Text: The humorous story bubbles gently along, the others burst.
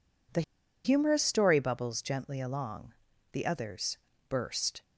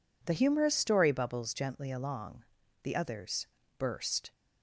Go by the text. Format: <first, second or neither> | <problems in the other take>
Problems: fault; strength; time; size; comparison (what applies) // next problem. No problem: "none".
second | pauses between "The" and "humorous"; at 0.4 s; 0.42 s long // pauses between "others" and "burst"; slight; at 3.9 s; 0.30 s long; slight in the second